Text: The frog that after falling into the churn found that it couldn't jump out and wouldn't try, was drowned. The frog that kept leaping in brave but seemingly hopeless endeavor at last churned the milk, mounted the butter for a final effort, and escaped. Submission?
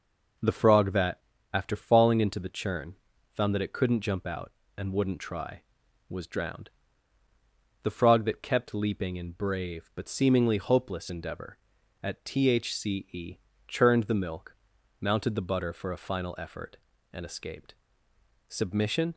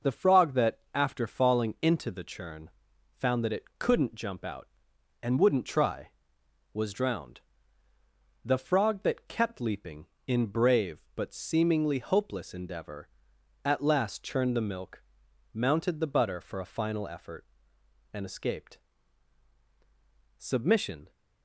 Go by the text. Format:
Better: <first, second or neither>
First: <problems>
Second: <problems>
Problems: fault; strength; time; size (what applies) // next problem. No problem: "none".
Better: second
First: pauses between "that" and "after"; slight; at 1.1 s; 0.34 s long // pauses between "churn" and "found"; at 2.9 s; 0.40 s long // says "thce" for "last"; at 12.2 s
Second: pauses between "churn" and "found"; at 2.7 s; 0.44 s long